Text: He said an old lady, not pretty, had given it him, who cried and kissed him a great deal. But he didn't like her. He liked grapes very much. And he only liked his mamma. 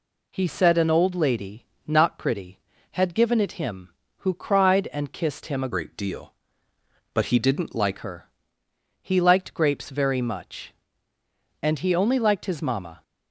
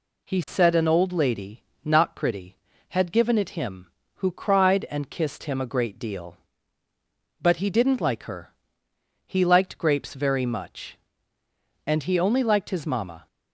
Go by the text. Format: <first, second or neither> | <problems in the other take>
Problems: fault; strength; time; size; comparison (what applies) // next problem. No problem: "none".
second | changes voice from "great" to "like"; from 5.7 to 7.9 s; 2.2 s long